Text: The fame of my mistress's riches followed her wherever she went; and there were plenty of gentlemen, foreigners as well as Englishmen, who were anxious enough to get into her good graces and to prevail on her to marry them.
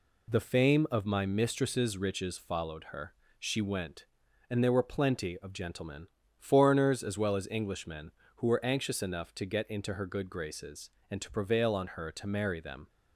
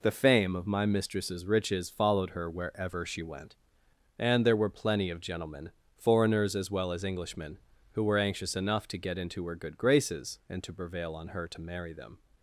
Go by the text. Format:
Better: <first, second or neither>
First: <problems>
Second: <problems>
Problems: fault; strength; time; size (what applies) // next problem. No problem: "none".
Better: second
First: skips "wherever"; at 3.2 s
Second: none